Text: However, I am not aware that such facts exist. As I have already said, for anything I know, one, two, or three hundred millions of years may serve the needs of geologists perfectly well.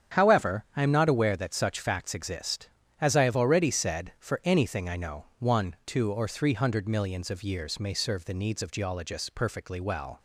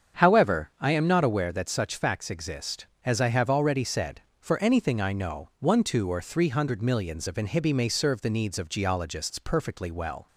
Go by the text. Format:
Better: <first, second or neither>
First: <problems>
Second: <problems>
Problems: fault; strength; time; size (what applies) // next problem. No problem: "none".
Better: first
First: starts louder than the rest; strong; until 1.2 s; 8.5 dB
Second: starts louder than the rest; strong; until 1.2 s; 7.5 dB // says "inhibi" for "years"; at 7.3 s